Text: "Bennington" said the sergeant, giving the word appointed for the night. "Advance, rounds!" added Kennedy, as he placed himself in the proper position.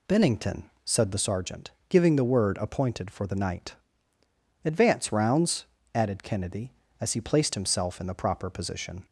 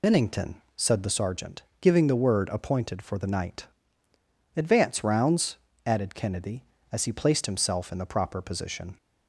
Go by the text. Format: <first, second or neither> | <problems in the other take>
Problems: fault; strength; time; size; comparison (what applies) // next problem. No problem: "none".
first | loses the start of "Bennington"; at 0.0 s; 50 ms